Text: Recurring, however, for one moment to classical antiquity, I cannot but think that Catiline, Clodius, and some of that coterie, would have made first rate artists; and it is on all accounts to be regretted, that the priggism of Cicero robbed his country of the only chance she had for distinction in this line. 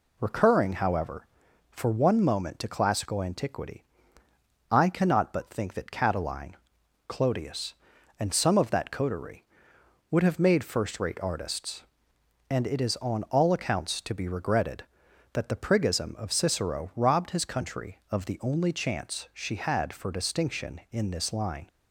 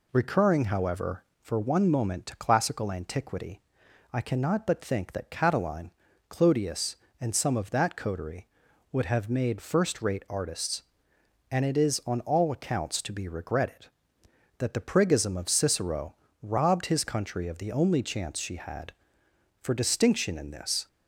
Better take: first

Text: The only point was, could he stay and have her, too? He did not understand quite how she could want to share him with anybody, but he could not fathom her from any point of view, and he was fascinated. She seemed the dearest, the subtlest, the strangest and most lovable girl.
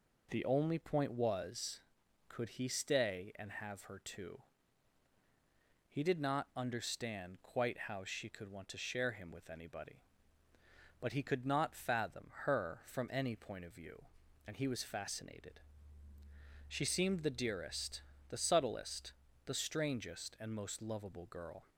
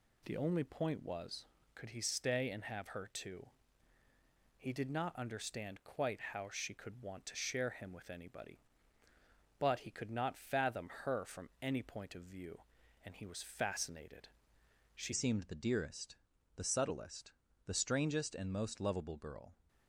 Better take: first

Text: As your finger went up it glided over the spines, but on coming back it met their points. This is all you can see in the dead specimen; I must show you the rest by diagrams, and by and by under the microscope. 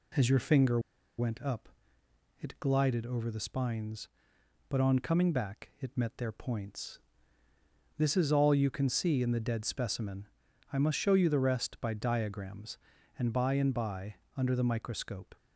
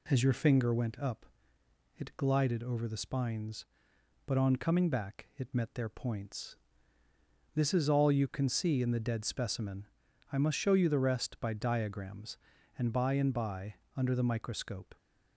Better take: second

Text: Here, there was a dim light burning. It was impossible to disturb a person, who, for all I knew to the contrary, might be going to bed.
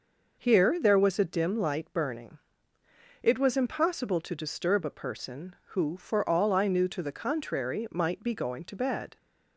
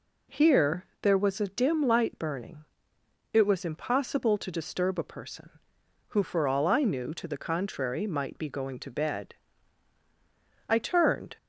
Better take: first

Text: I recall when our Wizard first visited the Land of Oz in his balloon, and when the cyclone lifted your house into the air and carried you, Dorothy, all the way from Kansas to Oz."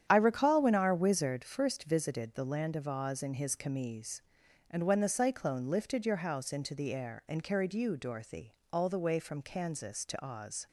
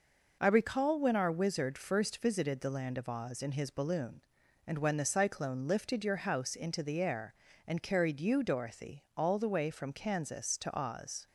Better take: second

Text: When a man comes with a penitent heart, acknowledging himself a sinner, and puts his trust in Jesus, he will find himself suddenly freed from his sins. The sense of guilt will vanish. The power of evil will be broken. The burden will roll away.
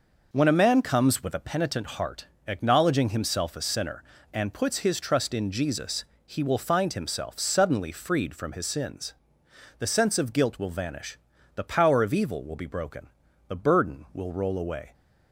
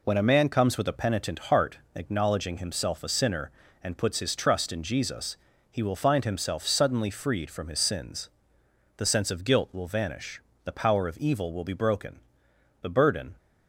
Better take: first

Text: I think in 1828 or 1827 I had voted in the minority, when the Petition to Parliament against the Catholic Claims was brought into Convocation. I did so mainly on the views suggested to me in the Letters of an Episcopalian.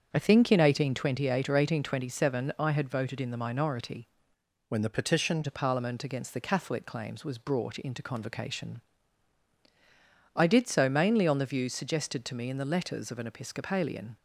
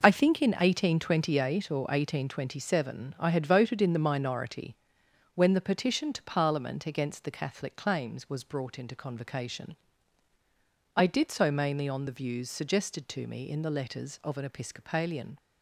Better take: second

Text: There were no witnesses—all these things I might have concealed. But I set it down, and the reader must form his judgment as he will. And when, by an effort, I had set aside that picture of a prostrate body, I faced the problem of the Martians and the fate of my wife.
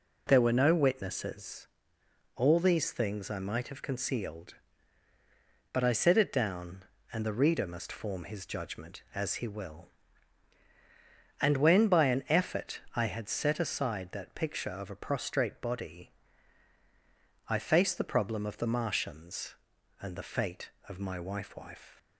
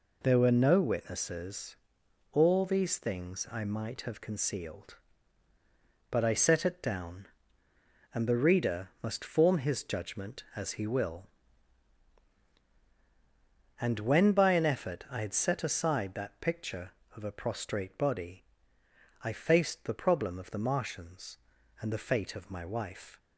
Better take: second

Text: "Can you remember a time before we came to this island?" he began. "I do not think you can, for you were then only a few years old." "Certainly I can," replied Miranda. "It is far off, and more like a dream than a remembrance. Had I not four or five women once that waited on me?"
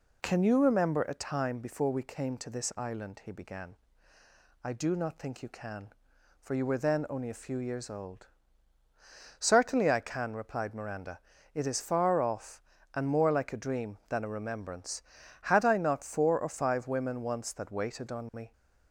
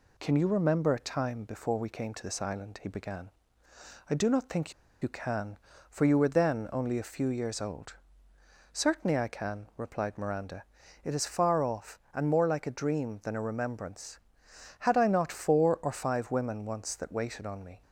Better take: first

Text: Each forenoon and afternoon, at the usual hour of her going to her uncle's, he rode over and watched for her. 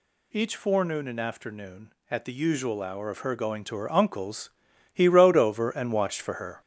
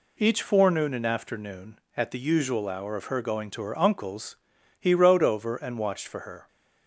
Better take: second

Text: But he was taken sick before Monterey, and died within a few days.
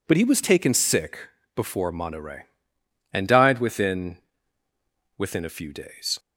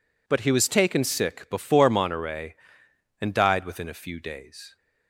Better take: second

